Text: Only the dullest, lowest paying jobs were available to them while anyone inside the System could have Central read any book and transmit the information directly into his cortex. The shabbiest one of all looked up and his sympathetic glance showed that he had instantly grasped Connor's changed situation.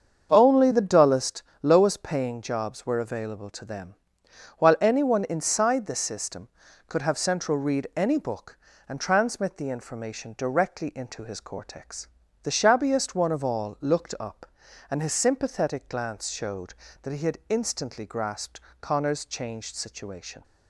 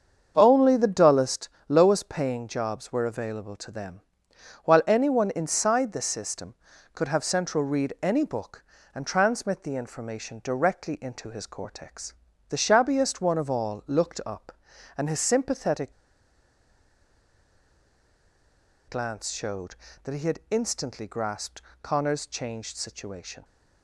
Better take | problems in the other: first | starts louder than the rest; until 1.3 s; 7 dB; also in the first // pauses between "them" and "while"; noticeable; at 4.0 s; 0.64 s long; noticeable in the first // pauses between "sympathetic" and "glance"; strong; at 15.9 s; 2.9 s long // pauses between "grasped" and "Connor's"; slight; at 21.6 s; 0.20 s long; slight in the first

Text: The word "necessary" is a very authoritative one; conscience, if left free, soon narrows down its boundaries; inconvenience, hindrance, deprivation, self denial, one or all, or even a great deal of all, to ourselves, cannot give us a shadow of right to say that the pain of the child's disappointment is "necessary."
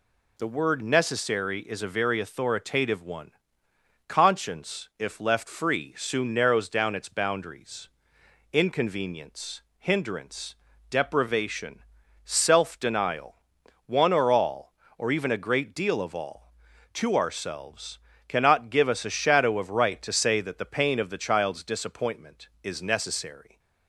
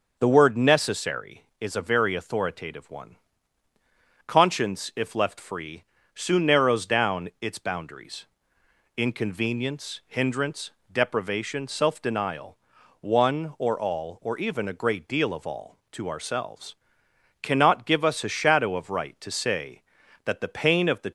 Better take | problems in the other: first | starts louder than the rest; until 1.2 s; 6 dB // stops before "child's disappointment is necessary"; at 21.0 s

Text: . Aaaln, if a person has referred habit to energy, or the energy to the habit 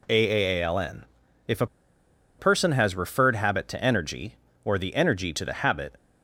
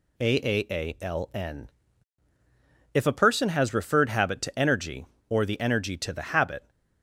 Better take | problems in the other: second | pauses between "a" and "person"; noticeable; at 1.6 s; 0.72 s long

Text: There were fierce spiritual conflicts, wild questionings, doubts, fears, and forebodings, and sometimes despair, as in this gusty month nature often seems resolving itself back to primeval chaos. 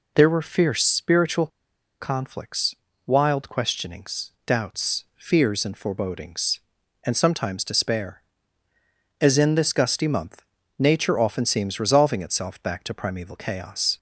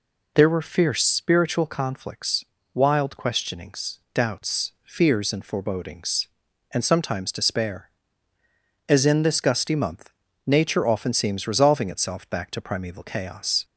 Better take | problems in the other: second | pauses between "spiritual" and "conflicts"; noticeable; at 1.4 s; 0.53 s long // pauses between "month" and "nature"; slight; at 10.4 s; 0.34 s long; slight in the second

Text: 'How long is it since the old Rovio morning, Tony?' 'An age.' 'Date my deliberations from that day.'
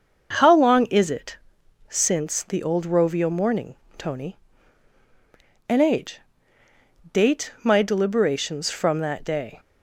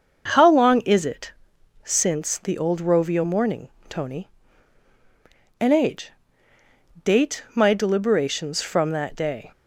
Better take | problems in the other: neither | starts louder than the rest; the same in both // pauses between "it" and "since"; noticeable; the same in both

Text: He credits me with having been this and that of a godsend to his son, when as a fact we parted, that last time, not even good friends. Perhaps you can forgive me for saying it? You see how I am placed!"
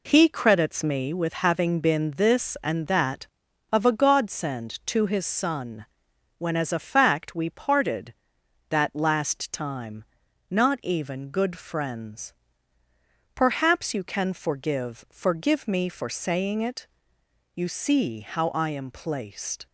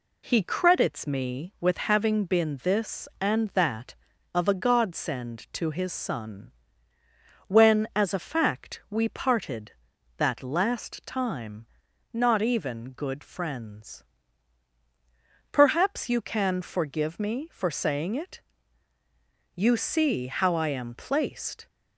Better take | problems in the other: second | says "forgive" twice; at 15.1 s

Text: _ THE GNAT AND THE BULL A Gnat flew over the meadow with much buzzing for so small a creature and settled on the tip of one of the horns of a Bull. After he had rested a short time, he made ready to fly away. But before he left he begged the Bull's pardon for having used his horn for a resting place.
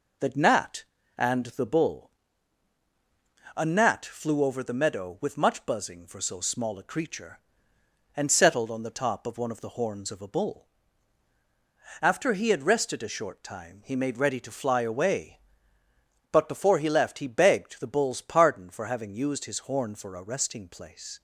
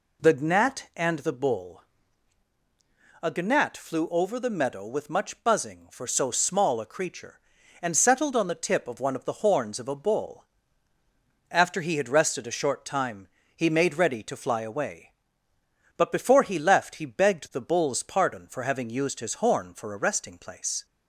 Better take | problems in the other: second | pauses between "BULL" and "A"; strong; at 2.0 s; 1.4 s long; strong in the second // says "top" for "tip"; at 8.9 s

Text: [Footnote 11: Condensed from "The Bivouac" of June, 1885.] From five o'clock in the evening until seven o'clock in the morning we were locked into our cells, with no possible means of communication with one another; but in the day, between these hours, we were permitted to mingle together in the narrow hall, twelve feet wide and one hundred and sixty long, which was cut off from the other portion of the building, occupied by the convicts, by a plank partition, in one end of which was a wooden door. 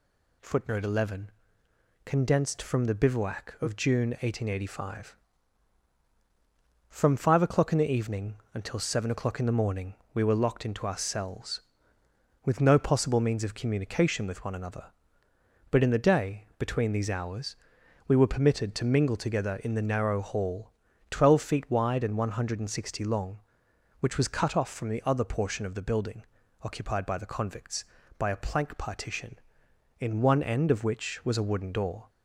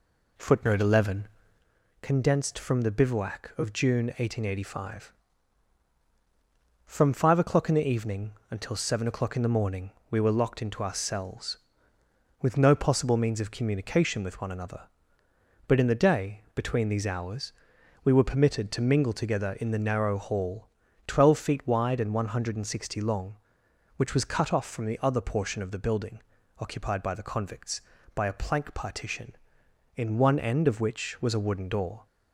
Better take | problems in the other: first | starts louder than the rest; slight; until 1.8 s; 2.5 dB // pauses between "evening" and "until"; slight; at 8.3 s; 0.18 s long; slight in the first // pauses between "morning" and "we"; slight; at 9.8 s; 0.22 s long; slight in the first

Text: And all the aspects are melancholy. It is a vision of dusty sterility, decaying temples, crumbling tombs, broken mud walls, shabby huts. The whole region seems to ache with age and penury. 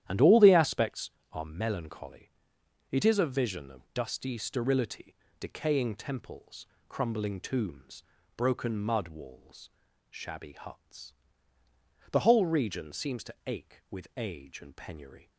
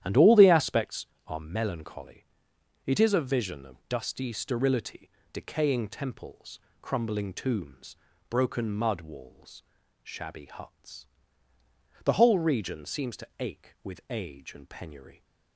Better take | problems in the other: neither | starts louder than the rest; strong; the same in both

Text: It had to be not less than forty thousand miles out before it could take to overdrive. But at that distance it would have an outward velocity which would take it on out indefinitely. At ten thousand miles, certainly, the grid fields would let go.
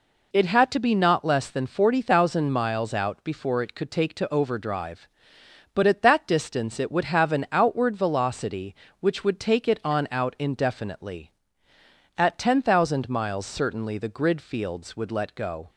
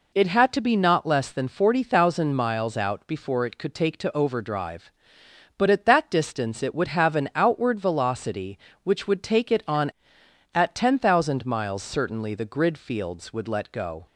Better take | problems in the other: first | skips "out indefinitely"; at 10.2 s

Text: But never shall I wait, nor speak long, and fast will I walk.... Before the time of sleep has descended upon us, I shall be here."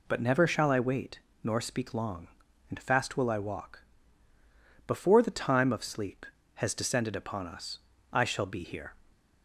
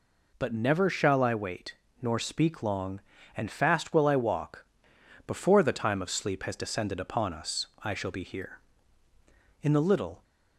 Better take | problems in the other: first | goes on to say "In the little"; noticeable; from 9.6 s on; 0.62 s long

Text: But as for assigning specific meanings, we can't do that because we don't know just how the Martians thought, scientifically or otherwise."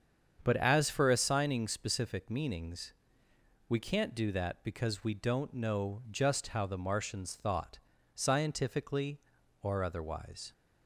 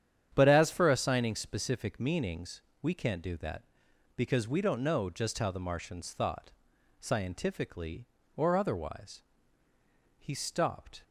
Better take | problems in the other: first | starts louder than the rest; strong; until 1.3 s; 9 dB; strong in the first // goes on to say "He stopped"; noticeable; from 10.1 s on; 0.86 s long

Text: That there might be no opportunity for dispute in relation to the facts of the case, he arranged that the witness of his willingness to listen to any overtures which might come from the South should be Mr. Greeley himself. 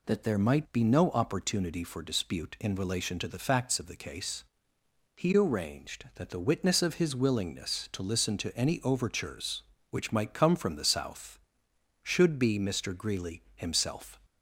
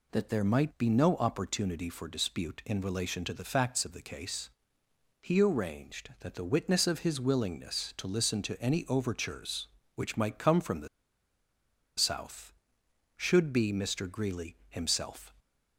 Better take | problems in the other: first | pauses between "the" and "South"; at 10.8 s; 1.1 s long

